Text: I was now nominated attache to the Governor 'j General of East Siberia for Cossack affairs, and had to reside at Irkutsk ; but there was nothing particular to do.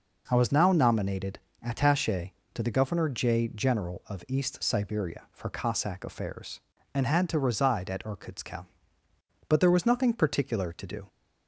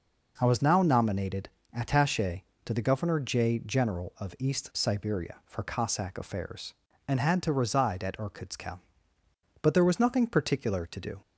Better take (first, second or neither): neither